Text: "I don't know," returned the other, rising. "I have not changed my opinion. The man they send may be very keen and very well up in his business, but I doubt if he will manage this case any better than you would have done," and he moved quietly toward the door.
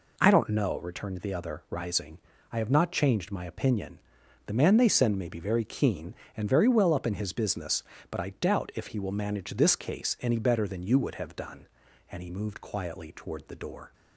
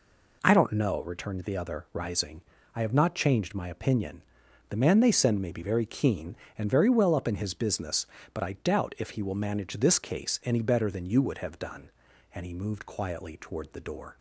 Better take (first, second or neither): neither